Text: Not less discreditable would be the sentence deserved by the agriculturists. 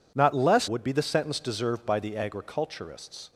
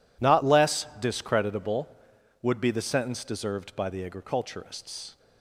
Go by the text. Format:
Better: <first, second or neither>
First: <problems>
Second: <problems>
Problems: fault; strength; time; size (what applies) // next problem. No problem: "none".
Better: second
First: skips "discreditable"; at 0.6 s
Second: none